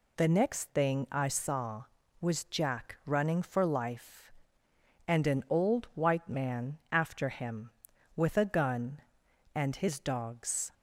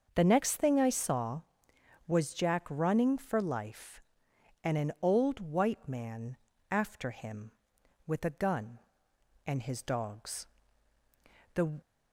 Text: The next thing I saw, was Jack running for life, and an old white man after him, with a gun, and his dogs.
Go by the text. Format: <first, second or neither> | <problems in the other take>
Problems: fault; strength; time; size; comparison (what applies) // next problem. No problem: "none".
first | starts louder than the rest; until 1.1 s; 6.5 dB // pauses between "man" and "after"; slight; at 6.3 s; 0.36 s long // goes on to say "The"; slight; from 11.5 s on; 0.26 s long